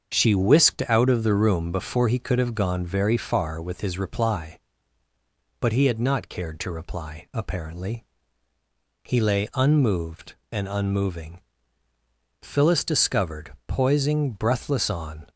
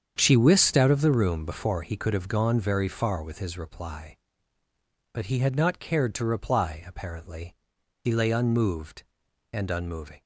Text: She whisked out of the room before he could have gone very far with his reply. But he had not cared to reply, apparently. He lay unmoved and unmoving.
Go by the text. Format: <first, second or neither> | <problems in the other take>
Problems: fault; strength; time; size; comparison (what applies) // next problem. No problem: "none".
second | starts louder than the rest; strong; until 1.1 s; 7 dB; strong in the second // goes on to say "Phyllis discovered poising breathless on"; strong; from 12.4 s on; 2.8 s long